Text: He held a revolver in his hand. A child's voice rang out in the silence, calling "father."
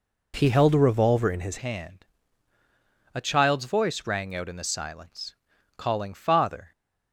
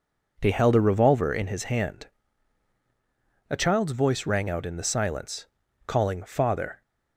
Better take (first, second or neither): second